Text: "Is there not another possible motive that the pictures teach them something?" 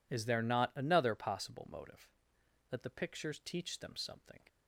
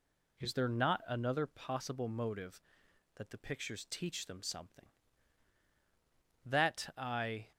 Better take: first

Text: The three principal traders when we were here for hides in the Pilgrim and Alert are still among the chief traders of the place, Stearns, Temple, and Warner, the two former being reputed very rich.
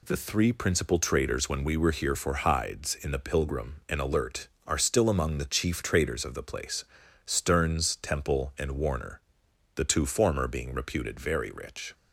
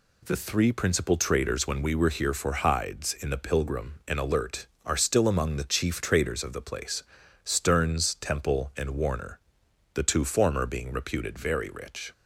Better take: neither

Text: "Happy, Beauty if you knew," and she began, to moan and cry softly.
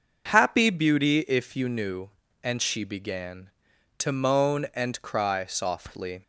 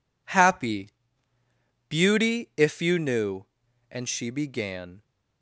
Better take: first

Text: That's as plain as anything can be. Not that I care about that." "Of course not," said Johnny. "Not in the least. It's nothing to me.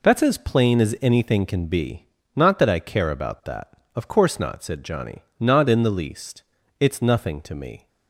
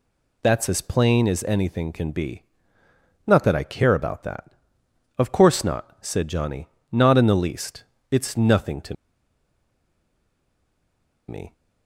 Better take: first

